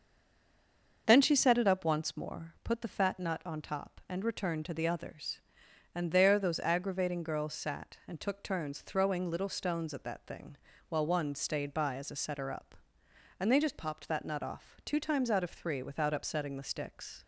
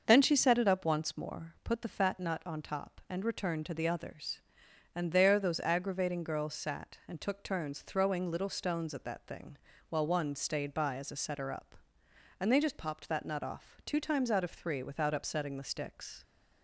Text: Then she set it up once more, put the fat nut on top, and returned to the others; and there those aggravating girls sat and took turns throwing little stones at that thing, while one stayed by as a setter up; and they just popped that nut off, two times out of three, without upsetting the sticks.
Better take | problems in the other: second | stays silent before the first word; until 1.0 s; 1.0 s long // starts louder than the rest; until 2.0 s; 6.5 dB; also in the second

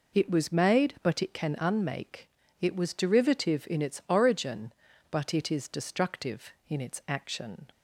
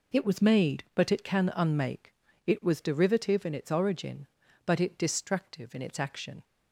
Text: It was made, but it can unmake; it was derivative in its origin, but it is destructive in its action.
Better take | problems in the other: first | skips "is"; at 4.9 s

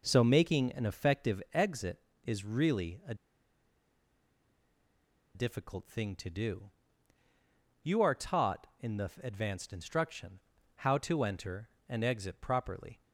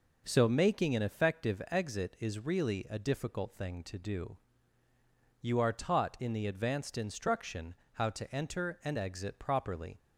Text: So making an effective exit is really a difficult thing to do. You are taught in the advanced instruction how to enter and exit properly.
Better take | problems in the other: second | pauses between "a" and "difficult"; strong; at 3.1 s; 2.2 s long // pauses between "instruction" and "how"; at 10.3 s; 0.38 s long; slight in the second

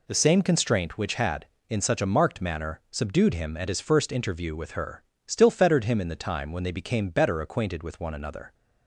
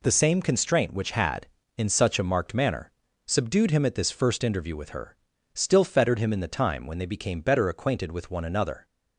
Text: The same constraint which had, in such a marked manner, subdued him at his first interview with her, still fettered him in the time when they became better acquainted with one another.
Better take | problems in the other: first | says "this" for "his"; at 3.9 s

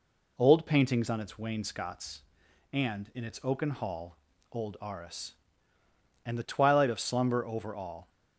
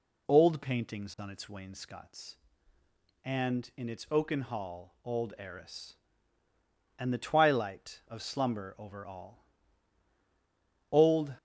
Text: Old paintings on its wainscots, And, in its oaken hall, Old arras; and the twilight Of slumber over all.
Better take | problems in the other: first | goes on to say "Old"; slight; from 10.9 s on; 0.42 s long

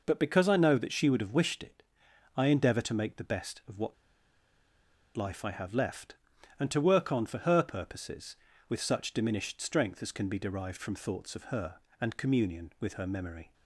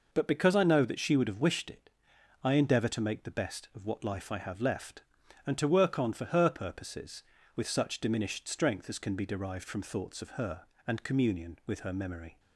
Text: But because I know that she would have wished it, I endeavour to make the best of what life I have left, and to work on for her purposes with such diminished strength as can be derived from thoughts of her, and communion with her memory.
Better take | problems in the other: second | pauses between "what" and "life"; at 3.9 s; 1.2 s long

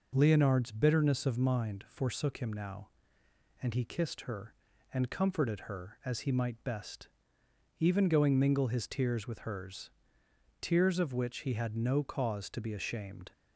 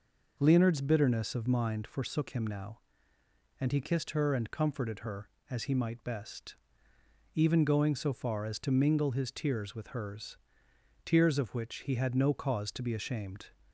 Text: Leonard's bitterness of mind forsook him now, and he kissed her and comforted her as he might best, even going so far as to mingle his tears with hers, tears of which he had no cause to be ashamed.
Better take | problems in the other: second | skips "so far as to"; at 8.3 s

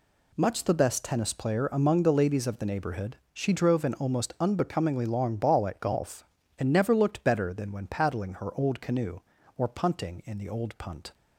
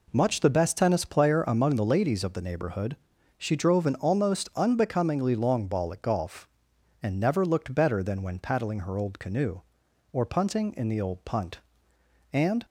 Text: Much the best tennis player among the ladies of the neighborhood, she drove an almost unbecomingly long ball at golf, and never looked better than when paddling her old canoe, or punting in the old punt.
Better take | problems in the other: first | goes on to say "And"; slight; from 12.3 s on; 0.32 s long

